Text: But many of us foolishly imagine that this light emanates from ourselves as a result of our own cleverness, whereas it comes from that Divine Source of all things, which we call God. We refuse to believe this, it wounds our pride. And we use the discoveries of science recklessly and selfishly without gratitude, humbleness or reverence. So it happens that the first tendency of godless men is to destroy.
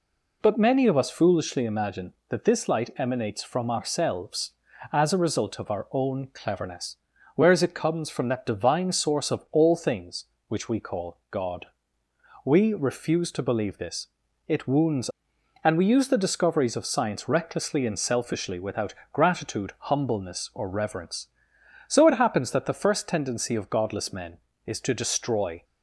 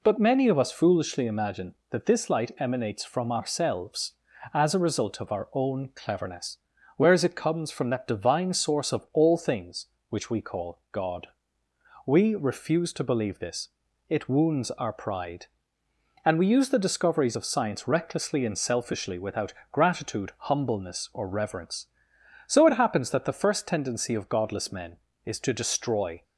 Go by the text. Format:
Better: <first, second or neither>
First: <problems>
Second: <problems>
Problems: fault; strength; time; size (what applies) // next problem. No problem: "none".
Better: second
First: skips "our pride"; at 15.3 s // pauses between "without" and "gratitude"; slight; at 18.9 s; 0.18 s long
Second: pauses between "without" and "gratitude"; slight; at 19.5 s; 0.18 s long